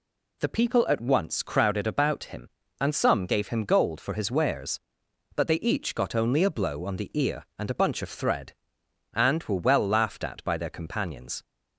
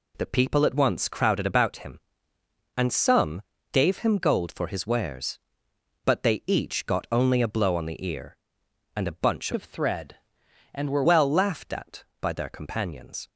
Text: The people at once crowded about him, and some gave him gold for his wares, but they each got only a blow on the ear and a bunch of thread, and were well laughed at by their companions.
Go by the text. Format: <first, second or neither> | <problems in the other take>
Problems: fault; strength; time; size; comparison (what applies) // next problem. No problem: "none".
first | pauses between "some" and "gave"; slight; at 3.4 s; 0.32 s long // changes voice from "of" to "were"; from 9.5 to 11.0 s; 1.5 s long